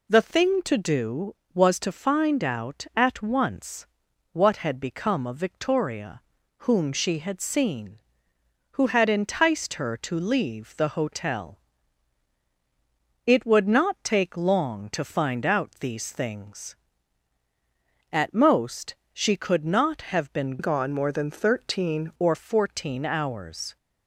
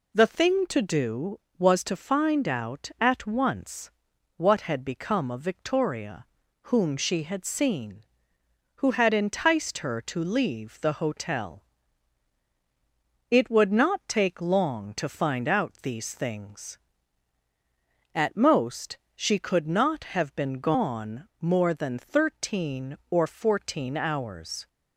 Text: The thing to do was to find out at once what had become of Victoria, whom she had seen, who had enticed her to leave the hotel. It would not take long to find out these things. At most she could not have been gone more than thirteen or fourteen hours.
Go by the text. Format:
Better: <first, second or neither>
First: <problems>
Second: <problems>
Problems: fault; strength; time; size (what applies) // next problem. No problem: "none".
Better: second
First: pauses between "once" and "what"; noticeable; at 3.8 s; 0.46 s long // pauses between "most" and "she"; slight; at 18.9 s; 0.18 s long // changes voice from "gone" to "thirteen"; from 20.5 to 22.1 s; 1.6 s long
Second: pauses between "once" and "what"; noticeable; at 3.9 s; 0.46 s long // pauses between "most" and "she"; slight; at 18.9 s; 0.18 s long